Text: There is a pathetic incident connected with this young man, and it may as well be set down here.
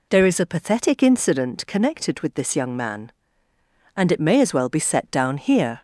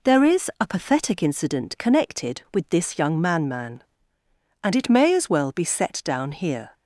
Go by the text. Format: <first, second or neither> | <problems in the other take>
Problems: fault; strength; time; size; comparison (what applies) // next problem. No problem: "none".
first | says "man" twice; at 3.4 s